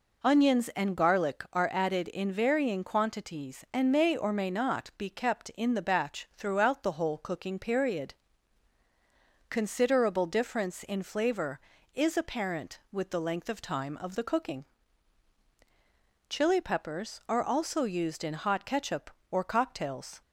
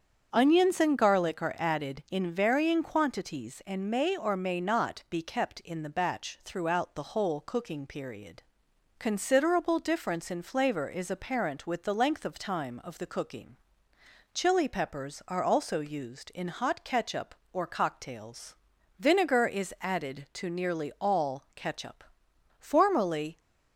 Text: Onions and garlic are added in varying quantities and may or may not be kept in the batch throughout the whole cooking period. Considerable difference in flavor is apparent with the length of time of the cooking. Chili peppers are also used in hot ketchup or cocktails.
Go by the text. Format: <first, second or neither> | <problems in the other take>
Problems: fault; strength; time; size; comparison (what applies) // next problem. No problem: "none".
first | starts louder than the rest; strong; until 1.3 s; 7.5 dB // goes on to say "Vinegar is added to nearly all ketchup Formerly"; strong; from 19.0 s on; 4.4 s long